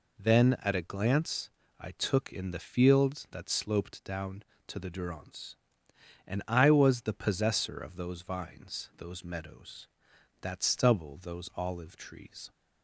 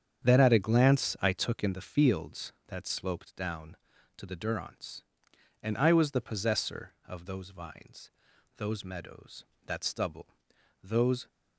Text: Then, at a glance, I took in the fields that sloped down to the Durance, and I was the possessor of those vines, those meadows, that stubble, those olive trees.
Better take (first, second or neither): first